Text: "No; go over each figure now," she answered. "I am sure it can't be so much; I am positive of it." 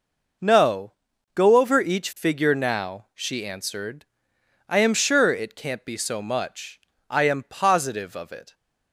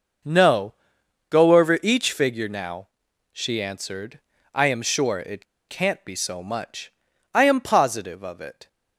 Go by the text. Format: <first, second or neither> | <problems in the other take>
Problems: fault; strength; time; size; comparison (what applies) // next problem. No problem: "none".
first | pauses between "it" and "can't"; slight; at 5.4 s; 0.24 s long